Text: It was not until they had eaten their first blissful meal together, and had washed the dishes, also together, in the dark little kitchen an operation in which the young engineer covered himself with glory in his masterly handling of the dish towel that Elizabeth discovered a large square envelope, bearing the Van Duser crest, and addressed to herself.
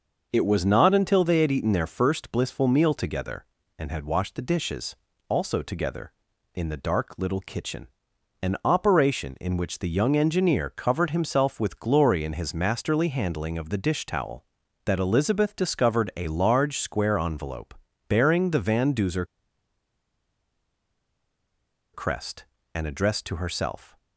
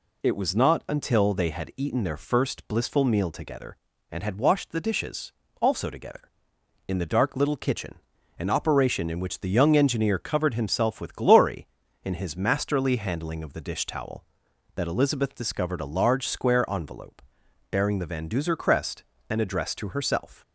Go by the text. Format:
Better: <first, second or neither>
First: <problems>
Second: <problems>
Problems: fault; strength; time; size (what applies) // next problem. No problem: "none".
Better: second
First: pauses between "kitchen" and "an"; noticeable; at 7.8 s; 0.54 s long // pauses between "Duser" and "crest"; strong; at 19.2 s; 2.6 s long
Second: pauses between "kitchen" and "an"; at 7.9 s; 0.44 s long